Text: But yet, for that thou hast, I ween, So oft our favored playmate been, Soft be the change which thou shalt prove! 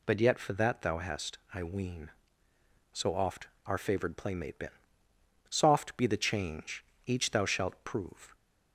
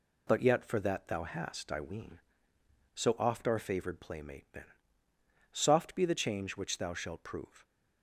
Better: second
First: pauses between "oft" and "our"; slight; at 3.4 s; 0.18 s long // says "each" for "which"; at 7.0 s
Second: none

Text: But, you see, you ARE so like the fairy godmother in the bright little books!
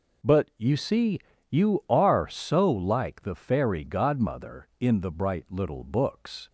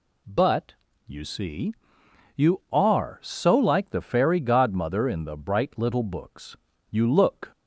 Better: first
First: none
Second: goes on to say "You look"; noticeable; from 6.8 s on; 0.62 s long

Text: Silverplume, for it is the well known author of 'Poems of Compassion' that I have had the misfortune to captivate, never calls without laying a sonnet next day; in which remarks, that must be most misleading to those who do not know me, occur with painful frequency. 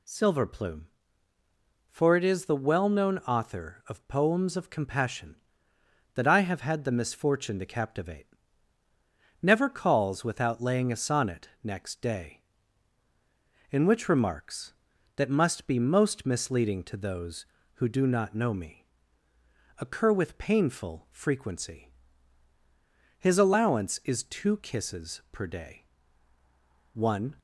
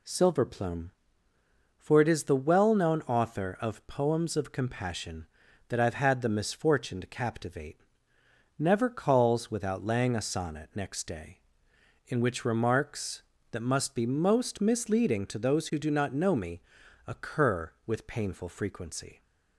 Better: second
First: goes on to say "His allowance is two kisses per day one"; strong; from 23.1 s on; 4.1 s long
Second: none

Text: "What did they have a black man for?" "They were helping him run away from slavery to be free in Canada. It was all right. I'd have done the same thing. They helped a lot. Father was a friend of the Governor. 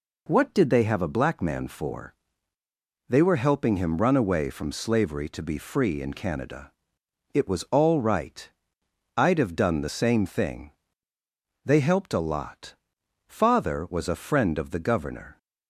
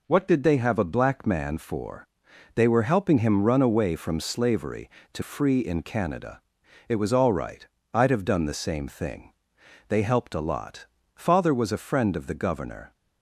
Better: first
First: none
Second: skips "be"; at 5.2 s

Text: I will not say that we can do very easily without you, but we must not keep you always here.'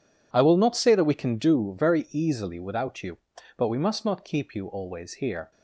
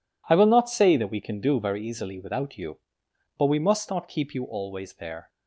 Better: first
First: none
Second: says "there" for "here"; at 4.9 s

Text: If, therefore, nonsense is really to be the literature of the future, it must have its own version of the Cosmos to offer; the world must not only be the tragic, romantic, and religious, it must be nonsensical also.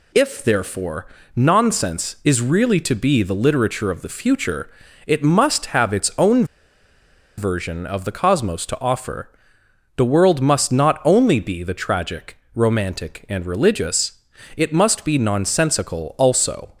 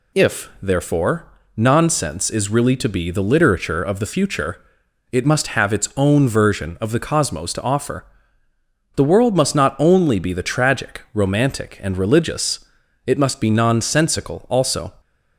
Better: second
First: pauses between "own" and "version"; noticeable; at 6.4 s; 0.93 s long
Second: none

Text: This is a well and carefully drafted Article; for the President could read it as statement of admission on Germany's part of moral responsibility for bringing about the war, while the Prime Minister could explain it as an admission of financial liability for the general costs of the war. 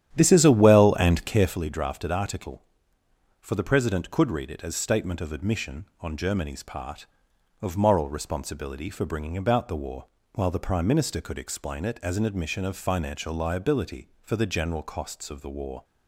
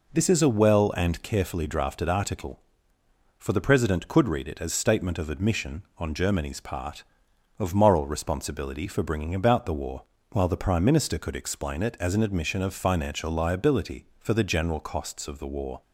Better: second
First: starts louder than the rest; strong; until 1.7 s; 10.5 dB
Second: none

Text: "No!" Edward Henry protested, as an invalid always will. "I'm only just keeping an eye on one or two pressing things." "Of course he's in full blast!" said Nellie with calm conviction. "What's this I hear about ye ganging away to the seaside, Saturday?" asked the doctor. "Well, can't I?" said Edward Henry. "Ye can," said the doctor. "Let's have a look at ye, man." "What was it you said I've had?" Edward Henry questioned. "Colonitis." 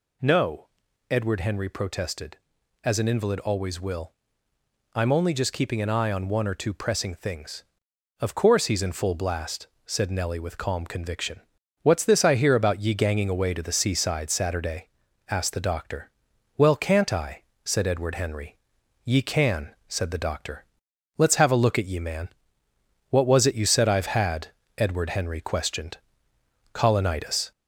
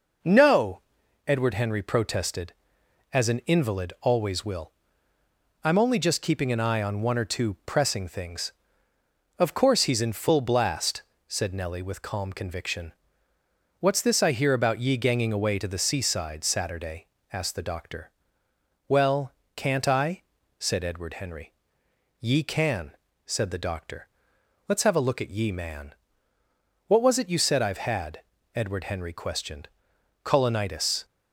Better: second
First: gets louder; slight; throughout; 2.5 dB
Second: none

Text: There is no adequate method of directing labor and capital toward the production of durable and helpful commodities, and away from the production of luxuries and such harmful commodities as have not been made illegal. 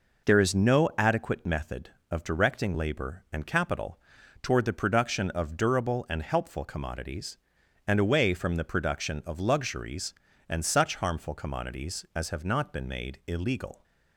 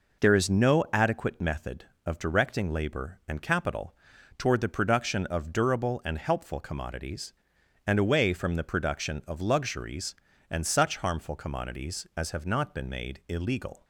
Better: neither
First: pauses between "capital" and "toward"; at 3.9 s; 0.42 s long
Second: pauses between "capital" and "toward"; at 3.9 s; 0.42 s long

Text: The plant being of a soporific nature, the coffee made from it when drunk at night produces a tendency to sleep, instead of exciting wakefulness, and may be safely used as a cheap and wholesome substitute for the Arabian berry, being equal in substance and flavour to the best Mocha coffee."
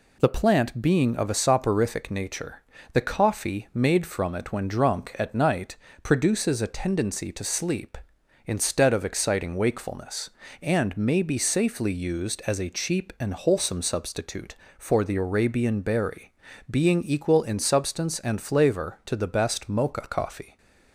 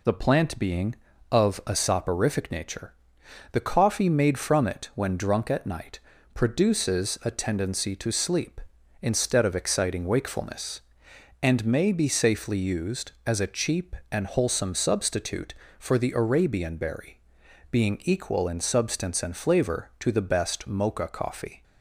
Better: neither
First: pauses between "night" and "produces"; slight; at 5.7 s; 0.26 s long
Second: pauses between "night" and "produces"; slight; at 5.9 s; 0.36 s long

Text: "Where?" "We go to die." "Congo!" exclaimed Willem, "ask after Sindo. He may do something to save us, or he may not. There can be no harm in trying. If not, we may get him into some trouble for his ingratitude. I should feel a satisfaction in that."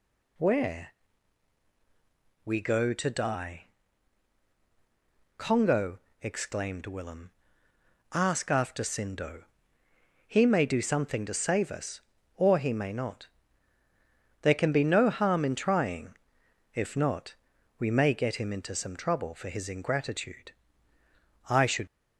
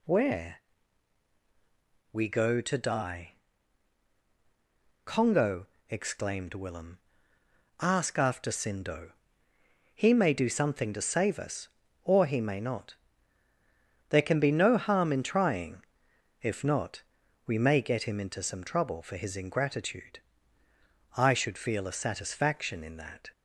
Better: second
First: stops before "feel a satisfaction in that"; at 21.8 s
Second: none

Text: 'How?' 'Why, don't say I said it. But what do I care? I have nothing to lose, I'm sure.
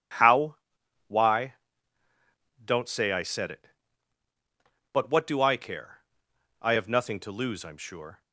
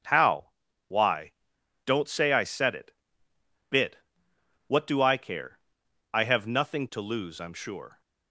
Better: first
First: none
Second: starts louder than the rest; until 1.9 s; 7 dB // says "Bit" for "But"; at 3.6 s

